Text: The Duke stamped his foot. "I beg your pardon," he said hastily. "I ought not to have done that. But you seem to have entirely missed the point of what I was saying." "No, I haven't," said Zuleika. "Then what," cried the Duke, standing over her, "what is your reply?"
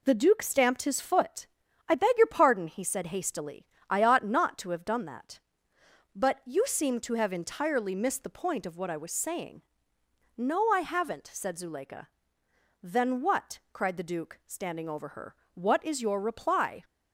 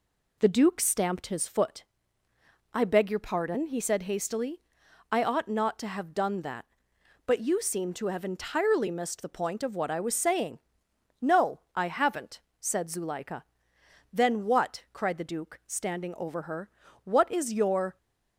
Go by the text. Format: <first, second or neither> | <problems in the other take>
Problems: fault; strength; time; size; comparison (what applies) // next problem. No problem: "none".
first | stops before "reply"; at 17.9 s